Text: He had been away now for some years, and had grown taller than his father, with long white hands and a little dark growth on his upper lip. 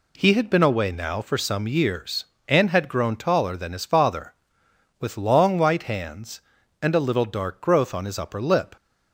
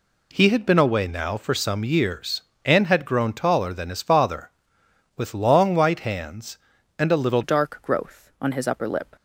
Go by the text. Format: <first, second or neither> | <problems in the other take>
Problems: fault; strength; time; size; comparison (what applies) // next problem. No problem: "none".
first | changes voice at "dark"; from 7.4 s on; 1.7 s long